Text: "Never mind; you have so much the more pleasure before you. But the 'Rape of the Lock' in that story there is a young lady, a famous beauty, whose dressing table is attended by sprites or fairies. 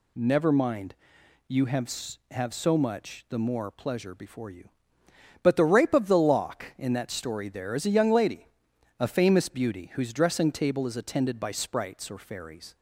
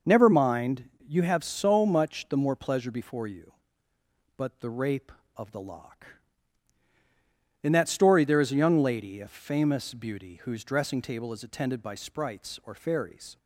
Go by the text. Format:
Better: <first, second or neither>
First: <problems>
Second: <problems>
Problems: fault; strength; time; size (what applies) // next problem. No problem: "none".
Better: second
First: says "have" twice; at 2.3 s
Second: none